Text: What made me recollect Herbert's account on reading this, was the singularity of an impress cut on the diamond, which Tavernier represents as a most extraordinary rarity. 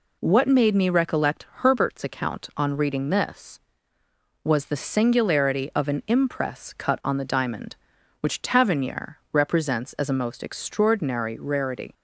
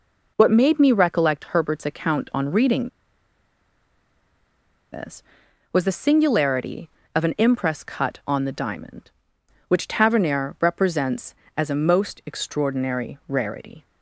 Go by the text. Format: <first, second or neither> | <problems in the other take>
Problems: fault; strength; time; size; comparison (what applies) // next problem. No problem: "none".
first | pauses between "reading" and "this"; strong; at 2.8 s; 2.0 s long